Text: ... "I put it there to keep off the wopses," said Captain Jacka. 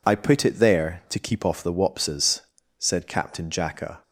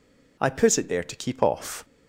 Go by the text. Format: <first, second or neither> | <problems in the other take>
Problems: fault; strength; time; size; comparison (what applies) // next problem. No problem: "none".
first | stops before "the wopses said Captain Jacka"; at 1.8 s